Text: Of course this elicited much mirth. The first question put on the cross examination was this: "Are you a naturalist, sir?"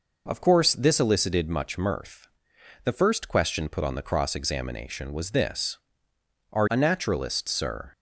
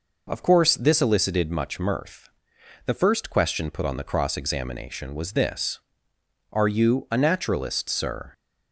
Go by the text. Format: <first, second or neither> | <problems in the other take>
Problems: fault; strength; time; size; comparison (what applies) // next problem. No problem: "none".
second | skips "you"; at 6.6 s